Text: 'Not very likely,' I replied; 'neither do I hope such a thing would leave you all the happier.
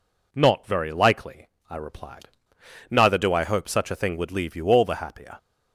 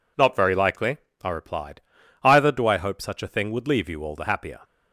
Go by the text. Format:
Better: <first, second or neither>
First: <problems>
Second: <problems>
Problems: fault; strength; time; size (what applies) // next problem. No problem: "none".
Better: first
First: none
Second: says "either" for "neither"; at 2.2 s